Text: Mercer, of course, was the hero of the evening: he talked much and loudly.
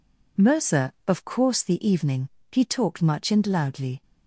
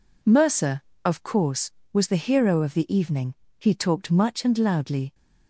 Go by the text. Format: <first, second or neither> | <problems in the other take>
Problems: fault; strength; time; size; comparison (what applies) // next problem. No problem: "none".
second | skips "was the hero of"; at 1.6 s